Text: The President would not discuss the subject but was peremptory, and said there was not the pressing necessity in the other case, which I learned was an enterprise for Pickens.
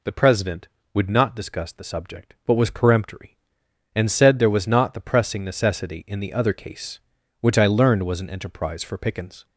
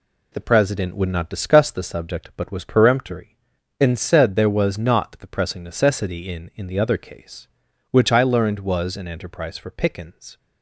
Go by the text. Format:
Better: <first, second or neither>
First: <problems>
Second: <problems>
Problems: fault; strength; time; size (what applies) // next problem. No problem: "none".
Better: first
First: none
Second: says "in" twice; at 6.5 s